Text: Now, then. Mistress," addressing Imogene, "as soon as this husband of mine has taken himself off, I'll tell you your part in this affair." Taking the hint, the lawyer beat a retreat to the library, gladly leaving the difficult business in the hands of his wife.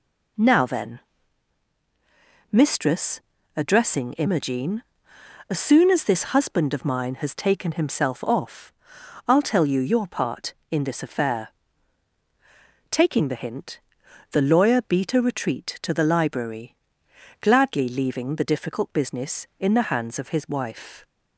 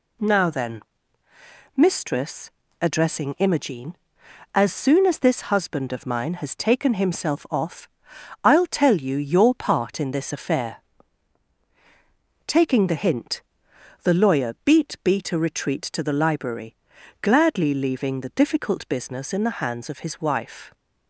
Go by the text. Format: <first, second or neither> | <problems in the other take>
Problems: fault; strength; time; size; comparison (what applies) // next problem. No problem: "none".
first | says "beat" twice; at 15.0 s